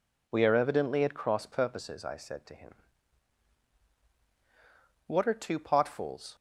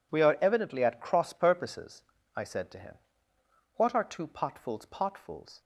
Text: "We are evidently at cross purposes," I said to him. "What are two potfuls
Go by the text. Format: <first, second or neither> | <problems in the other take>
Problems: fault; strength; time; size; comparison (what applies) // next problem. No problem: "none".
first | says "potfuls" twice; at 4.8 s